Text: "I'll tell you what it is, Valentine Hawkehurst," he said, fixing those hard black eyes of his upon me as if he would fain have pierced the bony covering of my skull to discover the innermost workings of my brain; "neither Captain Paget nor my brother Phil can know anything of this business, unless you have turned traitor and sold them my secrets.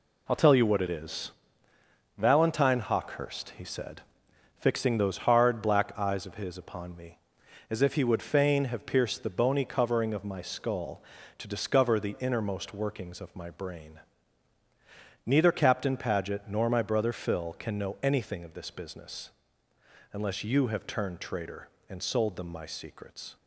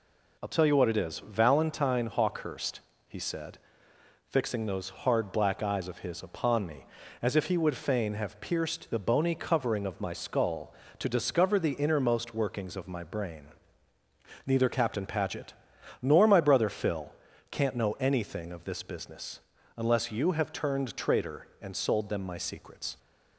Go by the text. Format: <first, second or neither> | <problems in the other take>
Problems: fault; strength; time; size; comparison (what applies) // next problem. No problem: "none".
first | pauses between "Paget" and "nor"; noticeable; at 15.5 s; 0.48 s long // says "can't" for "can"; at 17.4 s